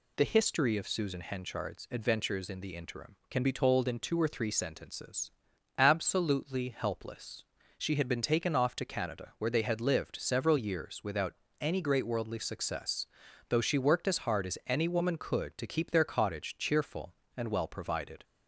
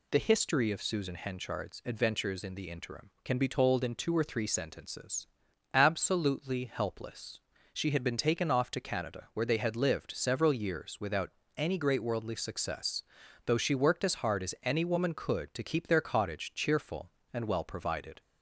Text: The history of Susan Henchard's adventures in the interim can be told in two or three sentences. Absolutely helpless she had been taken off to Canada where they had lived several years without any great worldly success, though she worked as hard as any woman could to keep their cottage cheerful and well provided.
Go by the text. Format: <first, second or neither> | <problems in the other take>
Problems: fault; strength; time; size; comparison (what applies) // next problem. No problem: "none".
neither | pauses between "helpless" and "she"; slight; the same in both // pauses between "without" and "any"; slight; the same in both